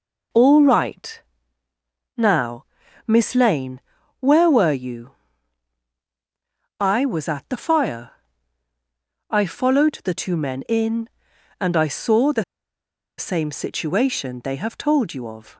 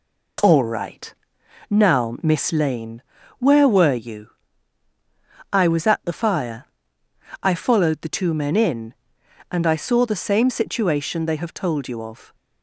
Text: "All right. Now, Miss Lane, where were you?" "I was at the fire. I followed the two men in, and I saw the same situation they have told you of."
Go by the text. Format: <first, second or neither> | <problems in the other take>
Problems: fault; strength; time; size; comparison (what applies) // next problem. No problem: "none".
second | pauses between "the" and "same"; noticeable; at 12.4 s; 0.74 s long